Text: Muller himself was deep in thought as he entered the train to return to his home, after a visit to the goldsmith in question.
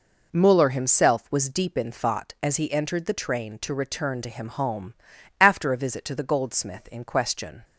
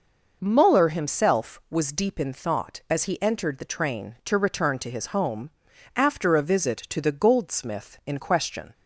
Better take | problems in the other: second | says "him" for "his"; at 4.2 s

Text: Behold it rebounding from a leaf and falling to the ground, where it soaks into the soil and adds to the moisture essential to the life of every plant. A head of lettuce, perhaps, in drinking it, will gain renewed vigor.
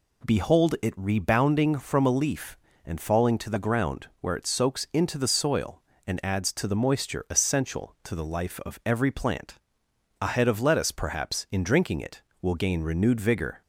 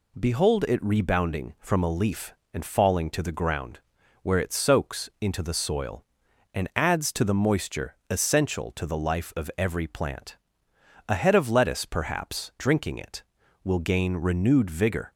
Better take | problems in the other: first | skips "in"; at 12.5 s

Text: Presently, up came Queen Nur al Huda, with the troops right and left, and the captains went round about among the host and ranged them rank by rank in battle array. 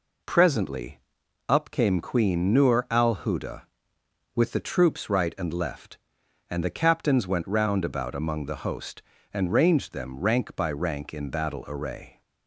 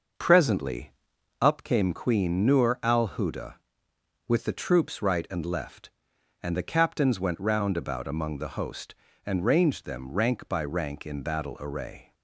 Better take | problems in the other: first | starts louder than the rest; noticeable; until 1.8 s; 6 dB

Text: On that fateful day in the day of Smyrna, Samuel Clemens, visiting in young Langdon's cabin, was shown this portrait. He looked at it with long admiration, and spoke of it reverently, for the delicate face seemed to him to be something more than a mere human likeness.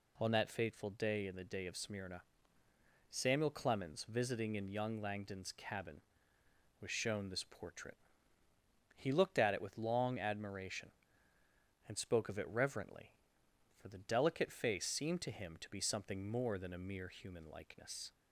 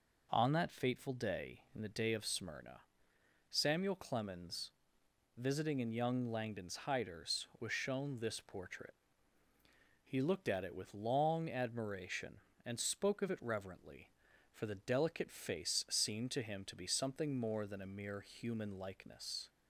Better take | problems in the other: first | says "hiders" for "cabin"; at 6.8 s

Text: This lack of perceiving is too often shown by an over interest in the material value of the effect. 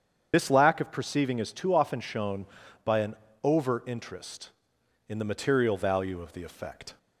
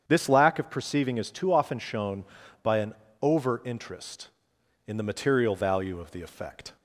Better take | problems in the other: second | loses the start of "This"; at 0.3 s; 45 ms // starts louder than the rest; strong; until 1.3 s; 8 dB; strong in the second // pauses between "an" and "over"; slight; at 3.1 s; 0.28 s long; slight in the second

